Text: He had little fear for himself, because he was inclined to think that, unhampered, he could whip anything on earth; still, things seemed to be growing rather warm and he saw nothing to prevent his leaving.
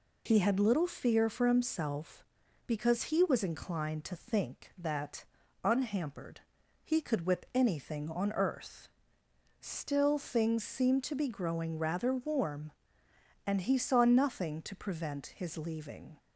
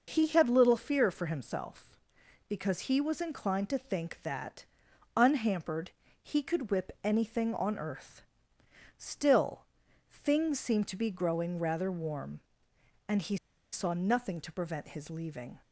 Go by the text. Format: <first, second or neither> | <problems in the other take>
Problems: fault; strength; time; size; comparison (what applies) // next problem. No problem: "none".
first | pauses between "he" and "saw"; slight; at 13.3 s; 0.35 s long